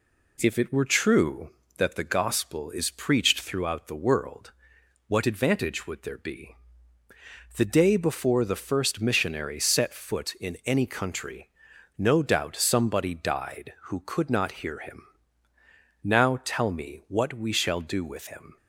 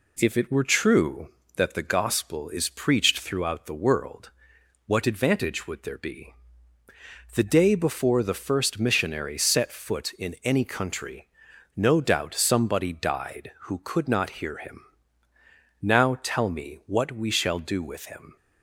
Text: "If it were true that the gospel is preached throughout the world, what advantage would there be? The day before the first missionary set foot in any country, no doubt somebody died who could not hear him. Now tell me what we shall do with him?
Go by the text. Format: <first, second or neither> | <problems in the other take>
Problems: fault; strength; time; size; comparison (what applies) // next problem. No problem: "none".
neither | none